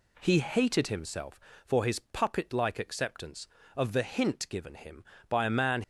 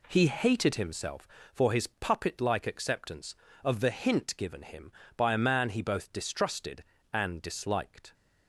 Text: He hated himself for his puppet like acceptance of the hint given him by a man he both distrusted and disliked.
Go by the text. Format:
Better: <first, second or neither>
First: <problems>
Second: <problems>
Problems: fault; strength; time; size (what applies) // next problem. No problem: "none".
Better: second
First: stops before "he both distrusted and disliked"; at 5.8 s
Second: none